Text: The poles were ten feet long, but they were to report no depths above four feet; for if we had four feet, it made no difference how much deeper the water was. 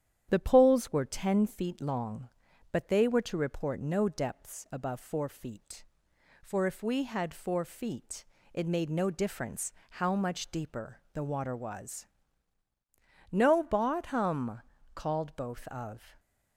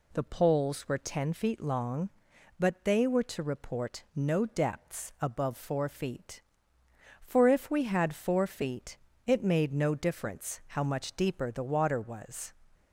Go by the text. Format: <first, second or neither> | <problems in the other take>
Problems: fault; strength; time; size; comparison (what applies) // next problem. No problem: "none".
second | starts louder than the rest; strong; until 1.3 s; 10 dB // pauses between "difference" and "how"; slight; at 9.7 s; 0.18 s long // goes on to say "No bottom called both of"; strong; from 13.3 s on; 2.8 s long